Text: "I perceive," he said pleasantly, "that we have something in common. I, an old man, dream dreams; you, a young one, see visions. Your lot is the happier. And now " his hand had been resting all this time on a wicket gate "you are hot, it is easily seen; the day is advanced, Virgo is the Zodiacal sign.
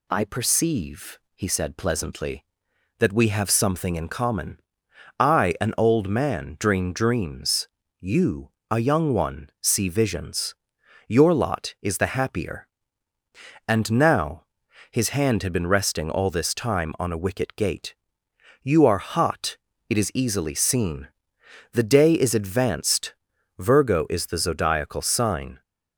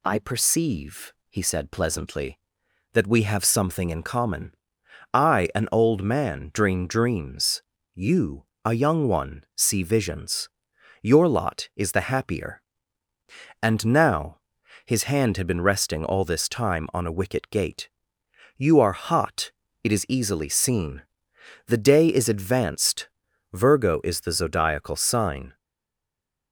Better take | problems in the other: first | pauses between "gate" and "you"; noticeable; at 17.8 s; 0.66 s long; noticeable in the first // stays silent after the last word; from 25.5 s on; 1.0 s long

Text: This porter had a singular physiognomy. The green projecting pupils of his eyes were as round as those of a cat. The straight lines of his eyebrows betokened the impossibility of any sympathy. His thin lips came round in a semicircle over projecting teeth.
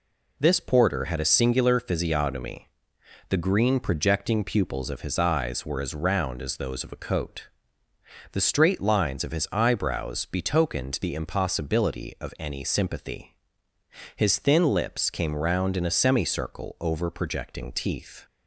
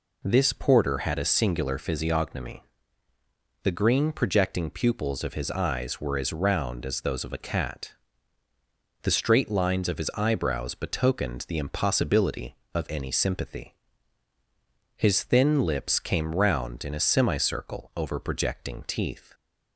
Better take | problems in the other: second | says "coat" for "cat"; at 6.9 s

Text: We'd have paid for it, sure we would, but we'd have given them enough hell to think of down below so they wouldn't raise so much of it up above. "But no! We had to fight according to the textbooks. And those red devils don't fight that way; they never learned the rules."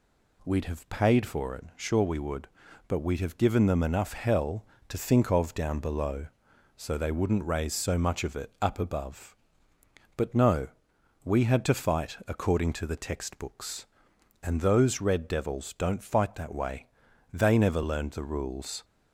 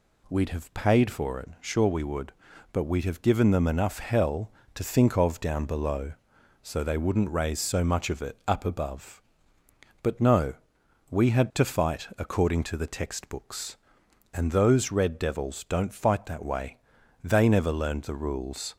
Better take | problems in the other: neither | none

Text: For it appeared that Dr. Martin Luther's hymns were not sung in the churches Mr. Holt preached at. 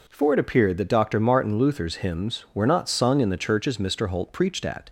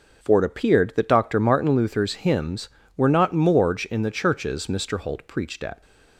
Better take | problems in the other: first | starts louder than the rest; noticeable; until 1.2 s; 6 dB // says "morge" for "sung"; at 3.3 s

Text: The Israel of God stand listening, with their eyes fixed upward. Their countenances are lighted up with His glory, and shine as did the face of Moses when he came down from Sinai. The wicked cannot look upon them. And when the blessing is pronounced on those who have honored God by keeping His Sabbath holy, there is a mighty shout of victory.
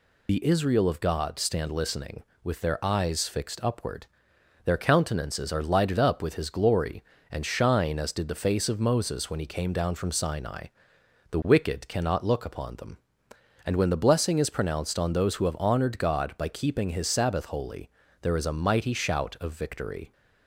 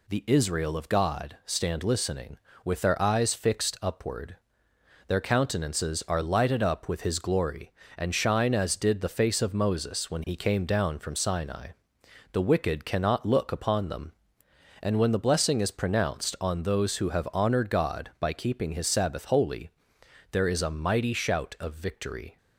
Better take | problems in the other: second | loses the start of "The"; at 0.2 s; 35 ms

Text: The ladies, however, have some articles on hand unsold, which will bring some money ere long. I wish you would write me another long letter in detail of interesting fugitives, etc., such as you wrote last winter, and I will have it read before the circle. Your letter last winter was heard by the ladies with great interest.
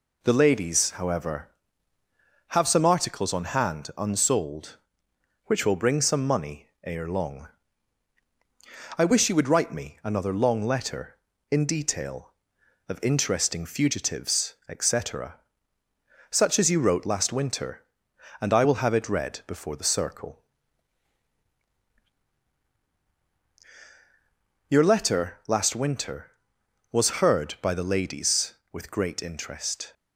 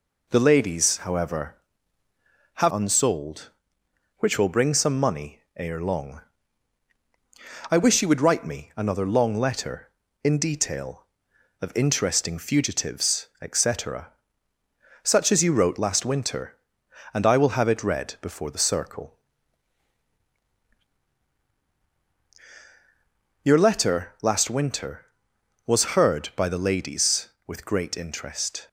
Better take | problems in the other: first | skips "some articles on hand"; at 2.7 s // pauses between "money" and "ere"; slight; at 5.3 s; 0.16 s long; slight in the first

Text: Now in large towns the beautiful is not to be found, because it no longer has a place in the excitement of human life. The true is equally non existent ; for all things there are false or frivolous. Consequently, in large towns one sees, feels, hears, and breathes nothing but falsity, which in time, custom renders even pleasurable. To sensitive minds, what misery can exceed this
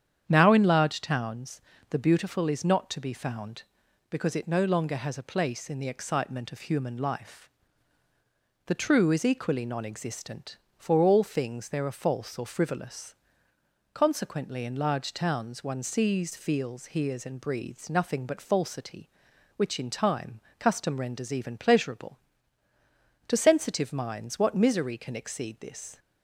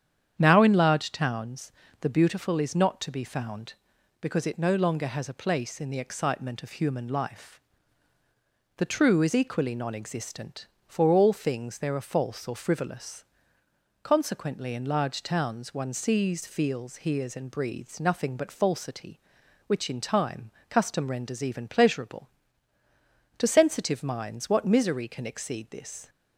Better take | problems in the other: neither | starts louder than the rest; strong; the same in both // pauses between "towns" and "the"; slight; the same in both

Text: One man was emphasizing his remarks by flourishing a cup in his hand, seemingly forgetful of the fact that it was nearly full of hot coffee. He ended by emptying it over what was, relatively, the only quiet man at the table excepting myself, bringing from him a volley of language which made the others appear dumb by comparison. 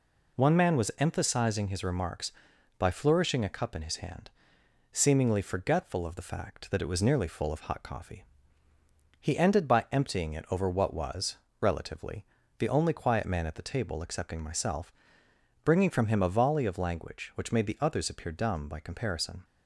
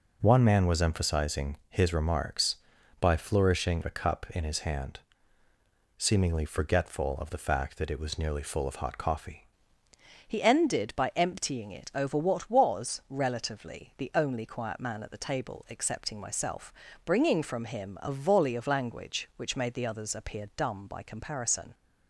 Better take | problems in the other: first | changes voice at "He"; from 10.2 s on; 11.5 s long

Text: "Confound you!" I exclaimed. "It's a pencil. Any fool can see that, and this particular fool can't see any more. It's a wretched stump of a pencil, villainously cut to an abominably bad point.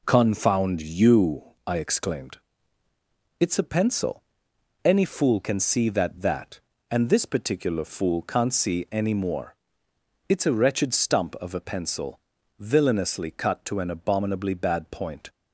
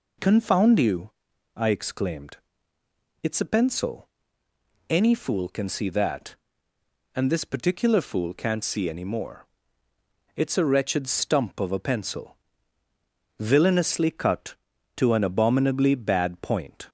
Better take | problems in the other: second | says "that" twice; at 6.1 s

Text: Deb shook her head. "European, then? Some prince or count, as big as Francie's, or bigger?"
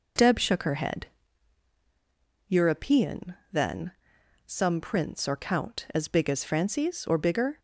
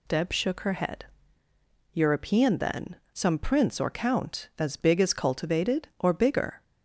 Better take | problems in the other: first | says "Cultivated" for "Francie's"; at 5.1 s

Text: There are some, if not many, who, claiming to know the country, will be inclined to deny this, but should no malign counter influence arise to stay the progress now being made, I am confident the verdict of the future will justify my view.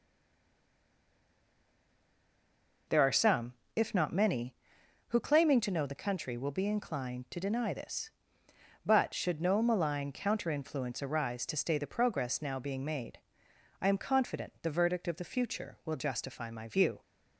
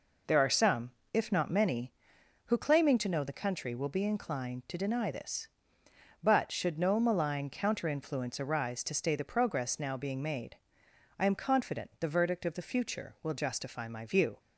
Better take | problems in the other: second | stays silent before the first word; strong; until 2.8 s; 2.8 s long

